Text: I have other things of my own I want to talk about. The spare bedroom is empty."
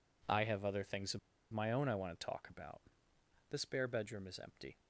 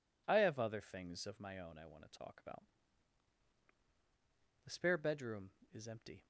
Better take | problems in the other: second | pauses between "of" and "my"; slight; at 1.1 s; 0.33 s long

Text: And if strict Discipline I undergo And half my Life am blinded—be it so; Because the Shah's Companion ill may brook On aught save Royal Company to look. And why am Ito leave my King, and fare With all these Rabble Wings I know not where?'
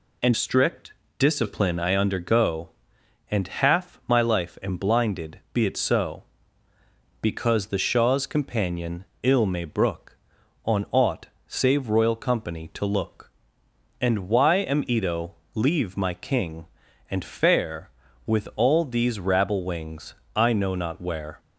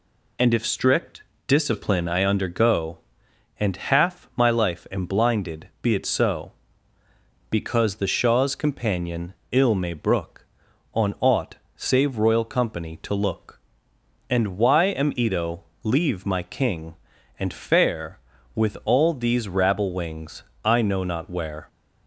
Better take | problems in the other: second | skips "if"; at 0.3 s // pauses between "strict" and "Discipline"; slight; at 0.9 s; 0.24 s long; slight in the second // pauses between "Companion" and "ill"; slight; at 9.0 s; 0.18 s long; slight in the second // pauses between "aught" and "save"; slight; at 11.2 s; 0.18 s long; slight in the second // pauses between "Ito" and "leave"; slight; at 15.3 s; 0.22 s long; slight in the second // pauses between "Wings" and "I"; slight; at 20.1 s; 0.22 s long; slight in the second

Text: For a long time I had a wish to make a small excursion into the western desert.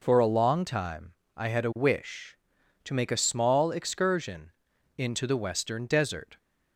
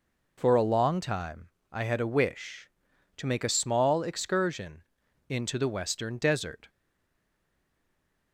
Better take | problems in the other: first | pauses between "time" and "I"; slight; at 1.4 s; 0.24 s long; slight in the first // pauses between "excursion" and "into"; noticeable; at 4.8 s; 0.46 s long; noticeable in the first // stays silent after the last word; noticeable; from 6.6 s on; 1.7 s long

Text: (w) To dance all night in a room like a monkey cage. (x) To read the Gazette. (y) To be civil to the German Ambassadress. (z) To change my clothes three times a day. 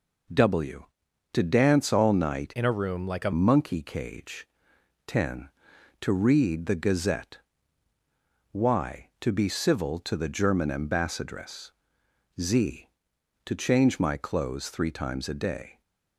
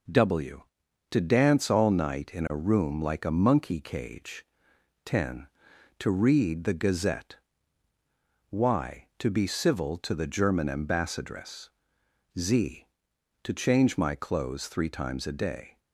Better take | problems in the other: second | changes voice from "in" to "a"; from 2.5 to 3.3 s; 0.8 s long

